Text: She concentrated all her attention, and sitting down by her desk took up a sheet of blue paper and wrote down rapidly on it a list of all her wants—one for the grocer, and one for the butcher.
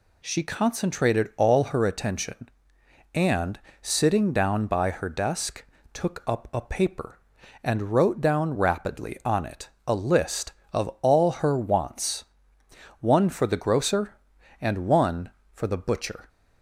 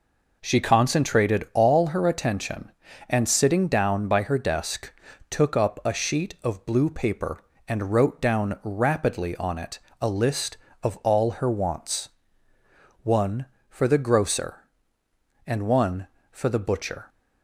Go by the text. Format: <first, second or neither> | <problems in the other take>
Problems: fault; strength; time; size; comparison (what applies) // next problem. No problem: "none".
second | pauses between "and" and "sitting"; slight; at 3.5 s; 0.24 s long // pauses between "desk" and "took"; slight; at 5.6 s; 0.28 s long; also in the second // skips "sheet of blue"; at 6.6 s // pauses between "it" and "a"; slight; at 9.6 s; 0.18 s long; slight in the second